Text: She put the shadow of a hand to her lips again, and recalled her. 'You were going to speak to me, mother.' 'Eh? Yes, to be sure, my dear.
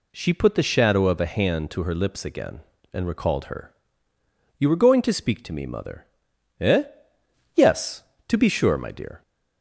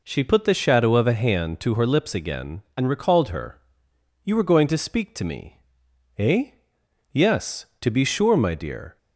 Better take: first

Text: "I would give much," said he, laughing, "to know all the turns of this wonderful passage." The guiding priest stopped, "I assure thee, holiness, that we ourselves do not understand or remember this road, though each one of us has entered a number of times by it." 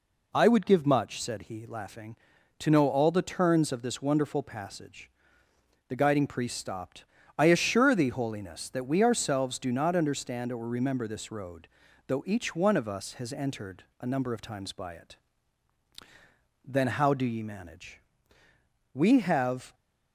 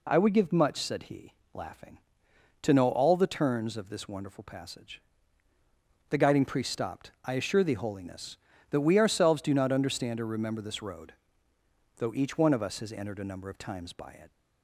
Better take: second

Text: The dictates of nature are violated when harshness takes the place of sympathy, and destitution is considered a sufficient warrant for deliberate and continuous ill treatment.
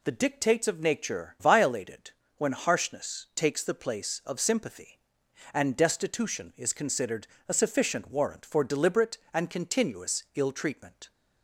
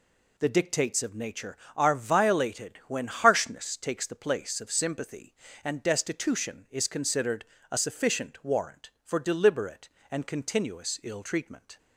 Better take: second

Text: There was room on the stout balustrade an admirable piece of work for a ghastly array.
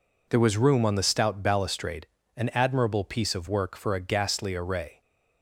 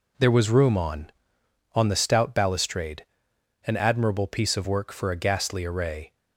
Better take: first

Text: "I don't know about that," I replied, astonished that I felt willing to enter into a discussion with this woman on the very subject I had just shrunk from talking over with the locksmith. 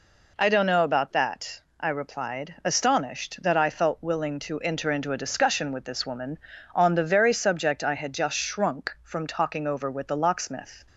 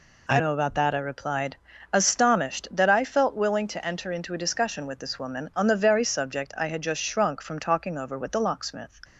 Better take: first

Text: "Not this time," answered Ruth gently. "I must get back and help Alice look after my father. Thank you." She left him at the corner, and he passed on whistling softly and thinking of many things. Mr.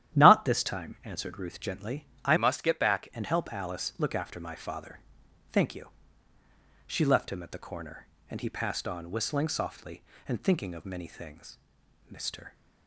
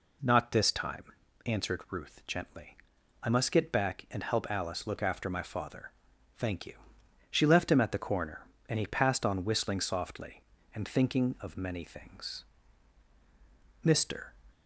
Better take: second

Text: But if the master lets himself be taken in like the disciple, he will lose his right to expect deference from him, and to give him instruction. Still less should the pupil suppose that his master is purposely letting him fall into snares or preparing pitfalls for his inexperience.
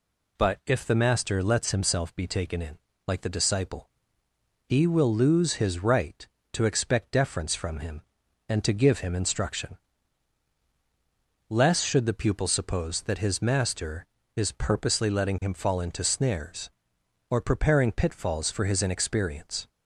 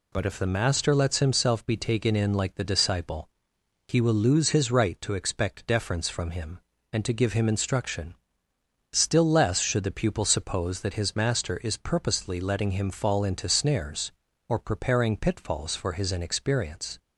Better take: second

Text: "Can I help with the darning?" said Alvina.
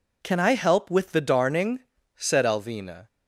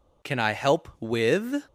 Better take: first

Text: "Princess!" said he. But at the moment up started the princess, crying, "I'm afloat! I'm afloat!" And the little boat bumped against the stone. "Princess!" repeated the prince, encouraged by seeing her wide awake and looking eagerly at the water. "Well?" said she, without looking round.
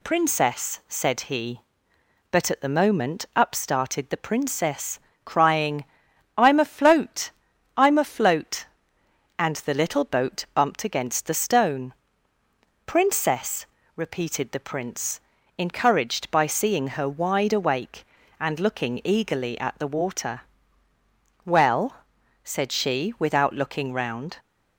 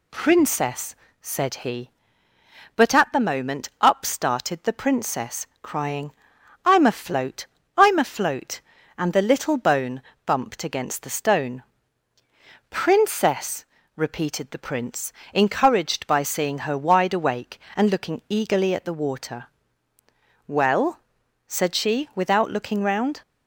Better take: first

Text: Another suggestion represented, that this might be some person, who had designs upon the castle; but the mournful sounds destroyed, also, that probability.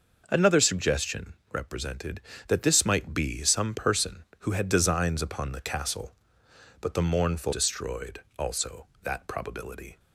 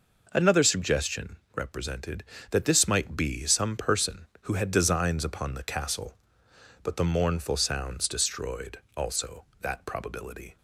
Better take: second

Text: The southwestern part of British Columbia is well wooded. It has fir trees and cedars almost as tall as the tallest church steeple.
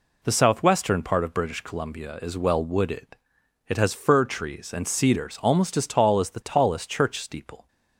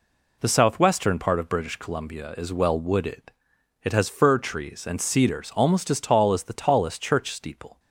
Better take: neither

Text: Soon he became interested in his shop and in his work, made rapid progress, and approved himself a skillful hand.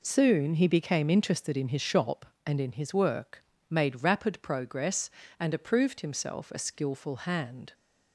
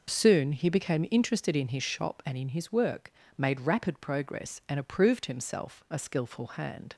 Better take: neither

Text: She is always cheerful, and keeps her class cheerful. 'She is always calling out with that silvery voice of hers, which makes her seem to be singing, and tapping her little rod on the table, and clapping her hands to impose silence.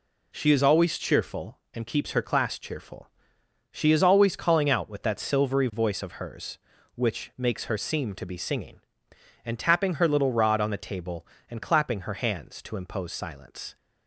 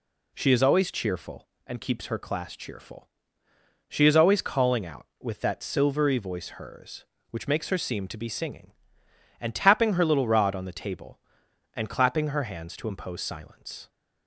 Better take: first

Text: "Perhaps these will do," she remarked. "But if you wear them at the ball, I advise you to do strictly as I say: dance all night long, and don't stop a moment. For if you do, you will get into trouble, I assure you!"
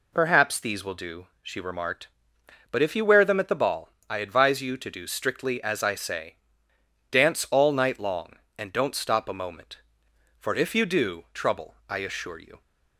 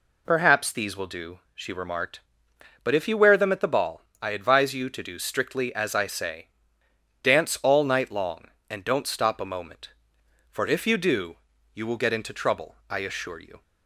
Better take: second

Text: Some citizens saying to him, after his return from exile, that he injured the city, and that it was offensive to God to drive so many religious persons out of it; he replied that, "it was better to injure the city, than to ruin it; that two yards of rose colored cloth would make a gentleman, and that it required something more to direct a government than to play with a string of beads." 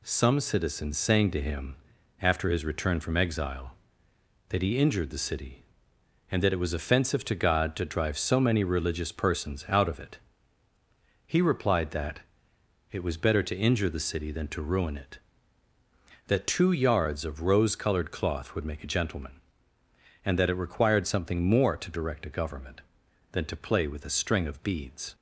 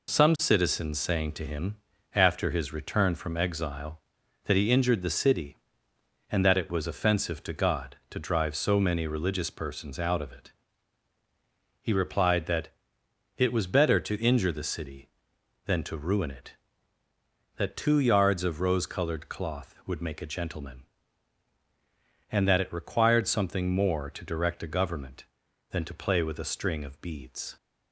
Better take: neither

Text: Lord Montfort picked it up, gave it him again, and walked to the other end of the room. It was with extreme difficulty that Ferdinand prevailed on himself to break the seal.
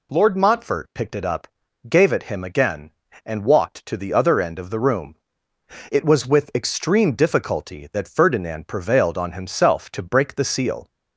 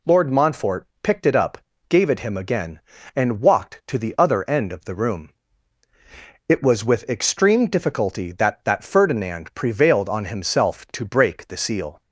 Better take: first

